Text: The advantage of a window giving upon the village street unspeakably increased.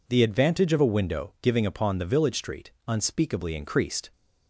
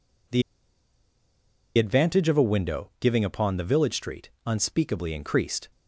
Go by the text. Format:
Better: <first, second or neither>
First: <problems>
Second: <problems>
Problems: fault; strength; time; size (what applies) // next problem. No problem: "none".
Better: first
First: pauses between "street" and "unspeakably"; slight; at 2.7 s; 0.18 s long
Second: pauses between "The" and "advantage"; strong; at 0.4 s; 1.3 s long // pauses between "street" and "unspeakably"; slight; at 4.2 s; 0.18 s long